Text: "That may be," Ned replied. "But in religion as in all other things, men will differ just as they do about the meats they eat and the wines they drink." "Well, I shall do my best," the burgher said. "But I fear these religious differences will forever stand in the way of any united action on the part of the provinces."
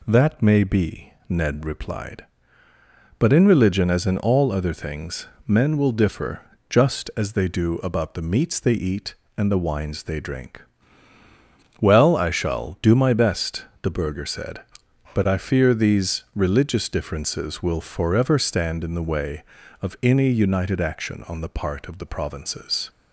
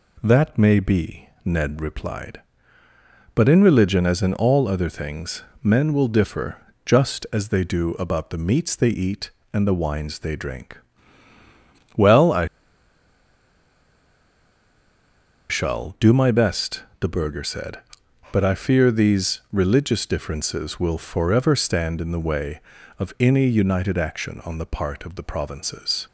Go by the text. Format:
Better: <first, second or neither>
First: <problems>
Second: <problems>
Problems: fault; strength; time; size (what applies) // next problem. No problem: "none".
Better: first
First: pauses between "differ" and "just"; slight; at 6.4 s; 0.28 s long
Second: pauses between "differ" and "just"; slight; at 6.5 s; 0.28 s long // pauses between "I" and "shall"; strong; at 12.4 s; 3.0 s long